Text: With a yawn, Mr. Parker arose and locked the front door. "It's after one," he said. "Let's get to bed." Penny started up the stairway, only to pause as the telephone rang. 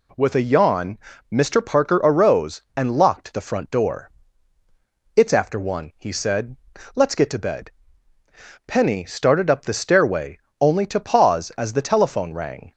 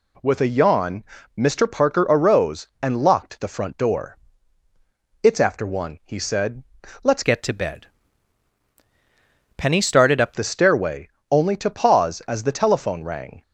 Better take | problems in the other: first | changes voice from "get" to "up"; from 7.2 to 10.3 s; 3.1 s long

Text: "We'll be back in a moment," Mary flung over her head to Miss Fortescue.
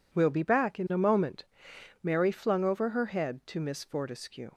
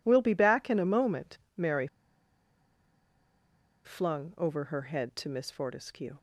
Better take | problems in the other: first | pauses between "Mary" and "flung"; strong; at 1.8 s; 1.9 s long

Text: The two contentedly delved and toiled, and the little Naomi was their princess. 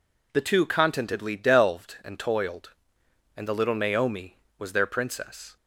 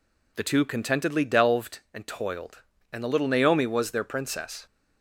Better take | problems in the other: neither | none

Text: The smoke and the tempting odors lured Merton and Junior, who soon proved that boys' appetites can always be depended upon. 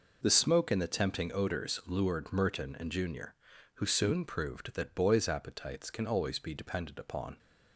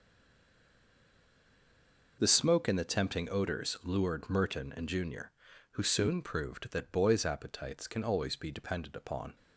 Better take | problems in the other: first | stays silent before the first word; until 2.1 s; 2.1 s long

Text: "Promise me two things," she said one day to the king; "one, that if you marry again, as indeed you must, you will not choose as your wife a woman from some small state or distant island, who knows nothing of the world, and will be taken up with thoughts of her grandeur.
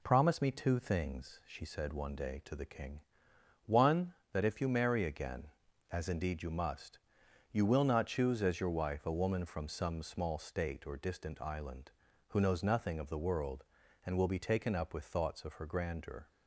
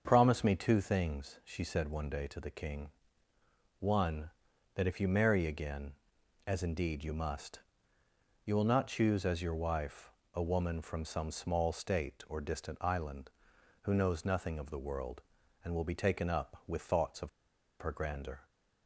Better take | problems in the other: first | starts louder than the rest; until 1.0 s; 6.5 dB // pauses between "wife" and "a"; slight; at 10.1 s; 0.20 s long // pauses between "of" and "her"; noticeable; at 17.2 s; 0.52 s long

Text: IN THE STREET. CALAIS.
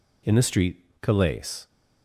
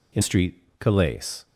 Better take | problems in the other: first | skips "THE"; at 0.2 s

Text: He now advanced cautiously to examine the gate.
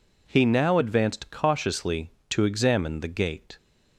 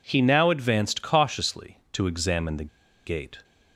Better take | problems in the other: first | pauses between "the" and "gate"; at 2.6 s; 0.37 s long

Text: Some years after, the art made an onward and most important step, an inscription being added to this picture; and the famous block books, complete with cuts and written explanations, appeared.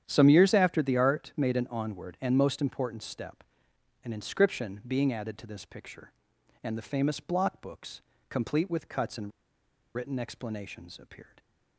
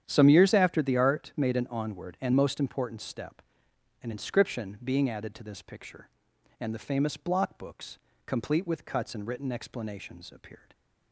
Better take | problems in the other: second | starts louder than the rest; strong; until 1.0 s; 9.5 dB; strong in the second // pauses between "and" and "written"; noticeable; at 9.3 s; 0.64 s long

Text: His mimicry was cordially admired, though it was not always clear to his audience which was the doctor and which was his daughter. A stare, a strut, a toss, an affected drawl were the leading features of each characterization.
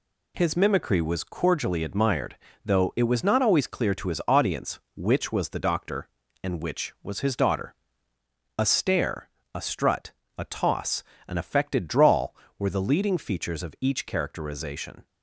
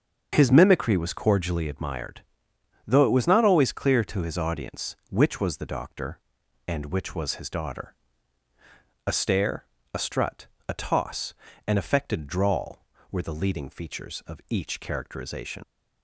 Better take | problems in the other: first | starts louder than the rest; until 1.3 s; 7 dB // leaves "characterization" unfinished; at 15.6 s; 60 ms

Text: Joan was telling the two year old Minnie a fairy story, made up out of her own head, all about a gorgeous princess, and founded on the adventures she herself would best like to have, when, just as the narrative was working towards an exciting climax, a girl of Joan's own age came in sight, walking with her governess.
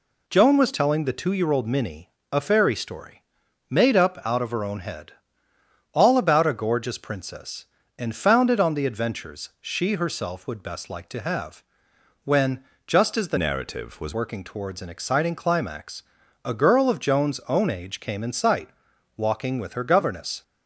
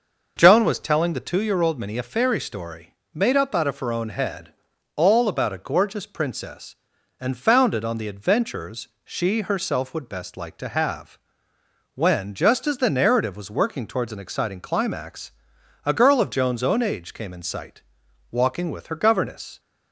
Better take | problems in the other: second | pauses between "Minnie" and "a"; slight; at 2.1 s; 0.22 s long // changes voice from "narrative" to "was"; from 13.3 to 14.1 s; 0.8 s long

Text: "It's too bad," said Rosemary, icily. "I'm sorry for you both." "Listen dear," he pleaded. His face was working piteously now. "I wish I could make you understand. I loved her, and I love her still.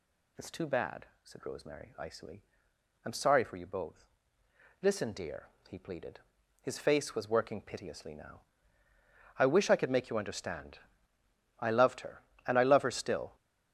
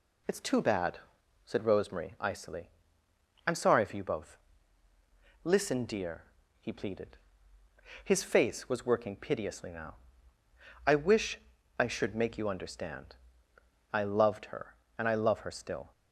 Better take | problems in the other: first | pauses between "wish" and "I"; at 11.3 s; 0.38 s long // says "should" for "could"; at 11.8 s

